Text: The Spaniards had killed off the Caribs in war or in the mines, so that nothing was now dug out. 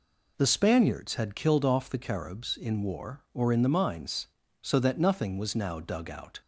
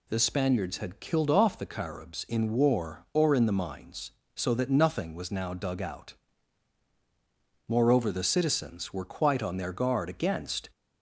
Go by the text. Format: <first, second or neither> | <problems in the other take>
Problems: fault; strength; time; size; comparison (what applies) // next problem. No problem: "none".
first | goes on to say "Moreover the citizens were quite on their guard against"; strong; from 7.6 s on; 3.0 s long